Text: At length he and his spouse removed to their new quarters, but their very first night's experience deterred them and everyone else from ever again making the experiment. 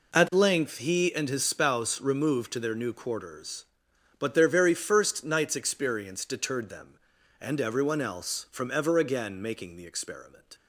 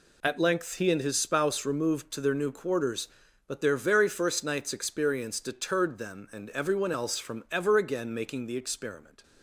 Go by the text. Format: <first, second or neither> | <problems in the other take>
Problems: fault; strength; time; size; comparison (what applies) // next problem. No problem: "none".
neither | none